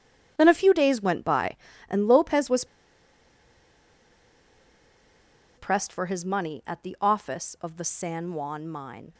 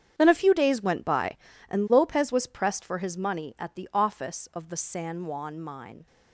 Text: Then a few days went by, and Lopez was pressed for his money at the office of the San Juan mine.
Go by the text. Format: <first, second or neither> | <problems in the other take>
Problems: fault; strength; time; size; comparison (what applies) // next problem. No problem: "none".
second | starts louder than the rest; strong; until 1.3 s; 8.5 dB; strong in the second // pauses between "was" and "pressed"; strong; at 2.6 s; 2.9 s long